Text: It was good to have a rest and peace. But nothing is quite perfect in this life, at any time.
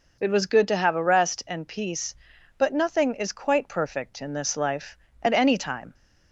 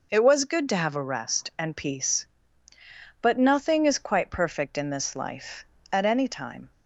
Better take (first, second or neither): neither